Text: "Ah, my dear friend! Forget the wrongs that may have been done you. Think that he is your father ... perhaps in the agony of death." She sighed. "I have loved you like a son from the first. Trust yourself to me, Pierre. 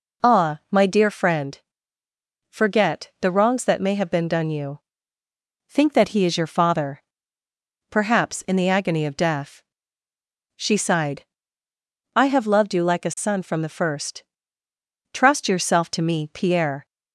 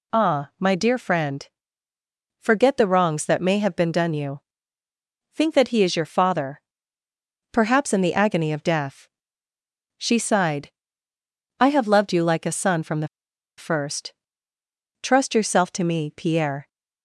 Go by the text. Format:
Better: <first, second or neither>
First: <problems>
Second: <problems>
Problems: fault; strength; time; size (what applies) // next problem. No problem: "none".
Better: first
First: none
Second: pauses between "the" and "first"; noticeable; at 13.0 s; 0.51 s long